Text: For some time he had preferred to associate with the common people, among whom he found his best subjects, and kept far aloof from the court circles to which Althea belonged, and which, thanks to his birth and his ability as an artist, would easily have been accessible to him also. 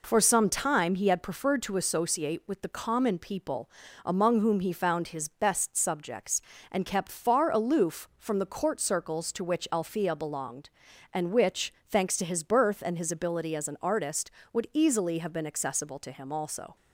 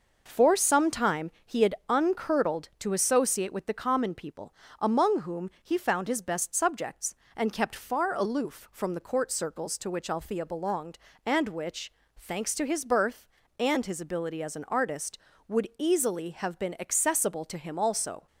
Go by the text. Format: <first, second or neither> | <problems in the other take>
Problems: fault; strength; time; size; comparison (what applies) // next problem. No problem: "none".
first | says "uncurdled" for "preferred"; at 1.8 s